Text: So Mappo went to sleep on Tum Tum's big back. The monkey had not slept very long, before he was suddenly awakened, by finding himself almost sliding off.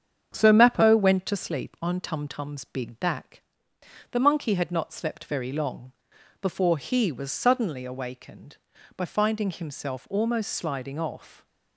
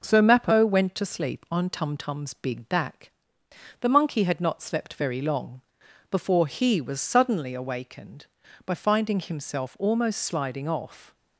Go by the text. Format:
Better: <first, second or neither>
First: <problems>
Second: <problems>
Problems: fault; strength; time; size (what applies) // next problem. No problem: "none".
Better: second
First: starts louder than the rest; strong; until 1.6 s; 7.5 dB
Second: none